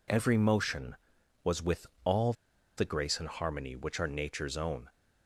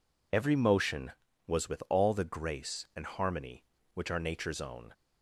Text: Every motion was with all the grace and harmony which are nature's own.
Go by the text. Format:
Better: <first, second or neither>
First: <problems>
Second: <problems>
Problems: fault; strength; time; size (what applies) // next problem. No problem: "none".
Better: second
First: pauses between "with" and "all"; slight; at 1.8 s; 0.18 s long // pauses between "all" and "the"; at 2.3 s; 0.44 s long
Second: none